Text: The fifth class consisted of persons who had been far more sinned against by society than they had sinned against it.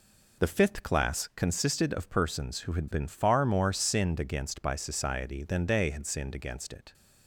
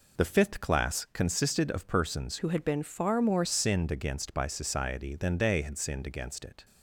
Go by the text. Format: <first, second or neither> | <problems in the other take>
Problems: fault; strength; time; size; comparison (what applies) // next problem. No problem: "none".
first | changes voice from "who" to "more"; from 2.3 to 3.4 s; 1.1 s long